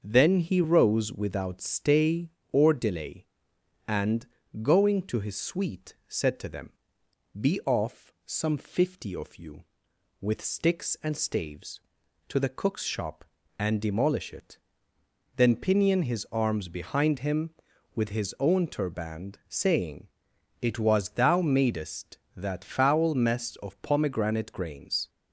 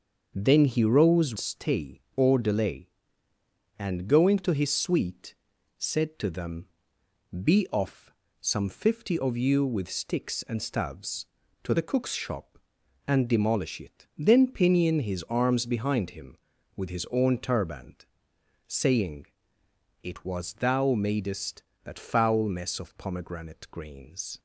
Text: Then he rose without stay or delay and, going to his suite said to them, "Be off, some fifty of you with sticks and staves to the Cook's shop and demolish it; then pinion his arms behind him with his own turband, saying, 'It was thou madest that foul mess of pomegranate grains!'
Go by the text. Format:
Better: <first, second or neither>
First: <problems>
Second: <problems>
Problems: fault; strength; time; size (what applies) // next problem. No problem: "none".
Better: first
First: starts louder than the rest; until 1.0 s; 6.5 dB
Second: starts louder than the rest; until 1.3 s; 6.5 dB // skips "without"; at 1.3 s // pauses between "suite" and "said"; at 5.3 s; 0.42 s long